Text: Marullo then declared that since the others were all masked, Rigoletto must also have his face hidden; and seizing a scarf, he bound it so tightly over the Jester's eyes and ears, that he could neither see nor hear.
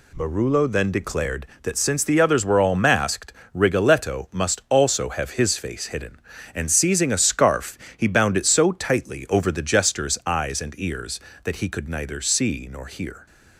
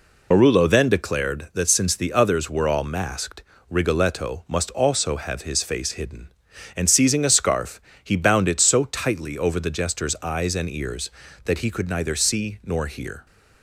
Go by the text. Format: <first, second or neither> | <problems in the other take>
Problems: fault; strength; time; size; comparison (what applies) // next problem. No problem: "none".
first | loses the start of "Marullo"; at 0.3 s; 70 ms